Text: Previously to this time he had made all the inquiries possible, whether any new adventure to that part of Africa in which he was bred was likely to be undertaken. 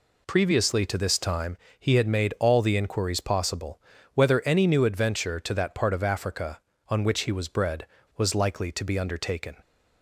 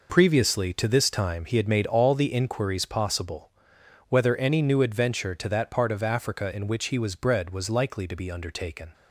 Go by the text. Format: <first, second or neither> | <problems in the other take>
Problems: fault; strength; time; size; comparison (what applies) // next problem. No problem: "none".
second | pauses between "time" and "he"; slight; at 1.5 s; 0.22 s long // says "on" for "in"; at 6.8 s